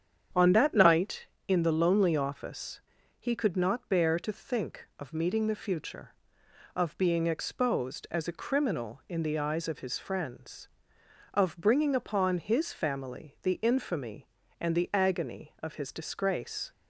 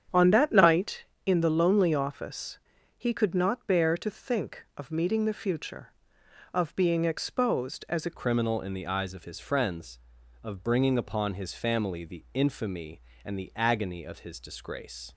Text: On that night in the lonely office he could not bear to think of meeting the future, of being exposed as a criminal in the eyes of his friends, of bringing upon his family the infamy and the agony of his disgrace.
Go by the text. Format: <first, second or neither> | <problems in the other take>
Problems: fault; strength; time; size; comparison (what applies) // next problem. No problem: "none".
first | starts louder than the rest; strong; until 1.3 s; 8.5 dB; strong in the first // pauses between "office" and "he"; at 2.5 s; 0.40 s long; also in the first // changes voice at "criminal"; from 8.1 s on; 7.0 s long